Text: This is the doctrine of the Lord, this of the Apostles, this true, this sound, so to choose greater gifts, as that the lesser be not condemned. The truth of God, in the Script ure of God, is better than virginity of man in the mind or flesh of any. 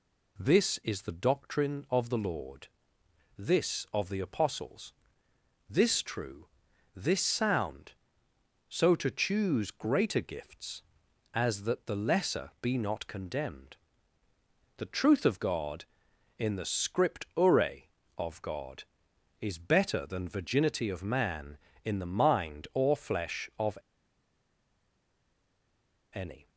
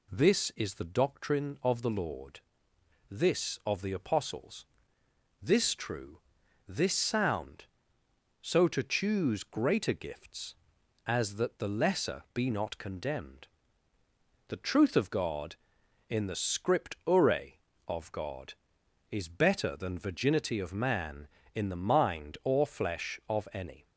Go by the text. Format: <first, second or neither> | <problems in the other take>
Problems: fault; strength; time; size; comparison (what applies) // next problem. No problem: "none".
second | pauses between "of" and "any"; strong; at 23.7 s; 2.3 s long